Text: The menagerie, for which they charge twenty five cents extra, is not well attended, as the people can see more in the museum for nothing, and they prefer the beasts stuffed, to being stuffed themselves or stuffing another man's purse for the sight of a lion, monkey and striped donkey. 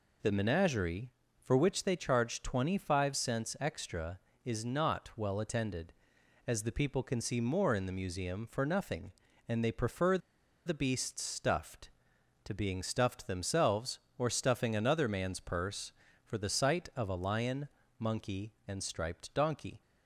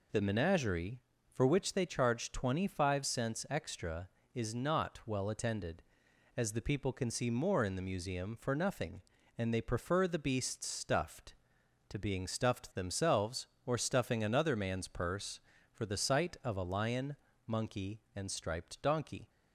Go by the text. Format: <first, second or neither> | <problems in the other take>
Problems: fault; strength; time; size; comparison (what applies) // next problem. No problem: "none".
second | pauses between "prefer" and "the"; noticeable; at 10.1 s; 0.47 s long